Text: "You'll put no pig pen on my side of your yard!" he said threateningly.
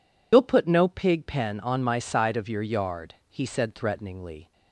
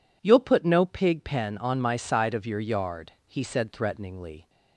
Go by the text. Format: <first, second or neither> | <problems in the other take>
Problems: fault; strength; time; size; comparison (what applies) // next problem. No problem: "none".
second | loses the start of "You'll"; at 0.3 s; 90 ms